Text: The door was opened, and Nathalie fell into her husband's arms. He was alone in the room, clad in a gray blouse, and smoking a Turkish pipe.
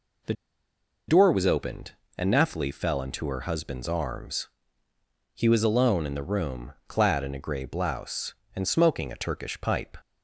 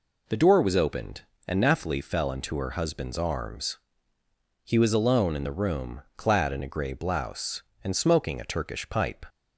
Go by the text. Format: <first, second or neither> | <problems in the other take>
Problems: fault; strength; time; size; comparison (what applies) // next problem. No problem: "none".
second | pauses between "The" and "door"; noticeable; at 0.3 s; 0.75 s long